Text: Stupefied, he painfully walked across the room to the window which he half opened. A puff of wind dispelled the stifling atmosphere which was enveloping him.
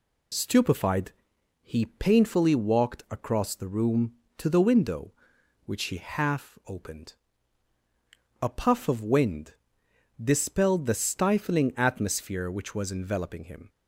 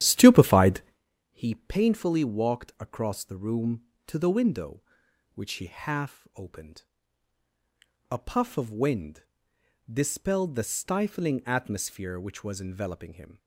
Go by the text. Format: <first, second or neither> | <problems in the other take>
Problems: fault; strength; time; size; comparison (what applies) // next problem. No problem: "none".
first | starts louder than the rest; strong; until 1.0 s; 11 dB // pauses between "wind" and "dispelled"; noticeable; at 9.2 s; 0.70 s long; noticeable in the first